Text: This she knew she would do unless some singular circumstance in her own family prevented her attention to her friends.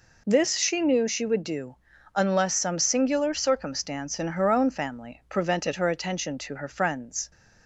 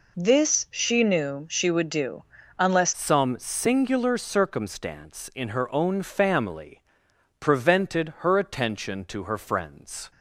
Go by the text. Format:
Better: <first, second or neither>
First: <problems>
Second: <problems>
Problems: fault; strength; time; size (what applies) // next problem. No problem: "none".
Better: first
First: pauses between "do" and "unless"; at 1.7 s; 0.40 s long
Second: pauses between "do" and "unless"; slight; at 2.2 s; 0.34 s long // changes voice at "some"; from 2.9 s on; 7.2 s long // pauses between "family" and "prevented"; noticeable; at 6.8 s; 0.58 s long